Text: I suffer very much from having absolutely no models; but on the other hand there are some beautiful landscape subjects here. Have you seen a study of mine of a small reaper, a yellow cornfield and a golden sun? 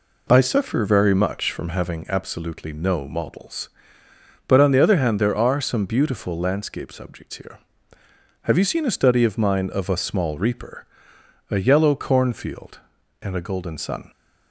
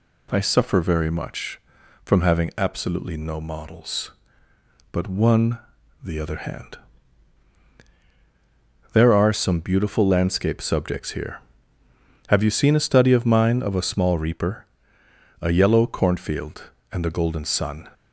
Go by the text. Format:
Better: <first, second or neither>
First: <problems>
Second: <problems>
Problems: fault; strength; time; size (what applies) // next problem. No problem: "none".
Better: first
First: none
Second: says "one" for "on"; at 5.0 s // pauses between "hand" and "there"; strong; at 6.7 s; 2.1 s long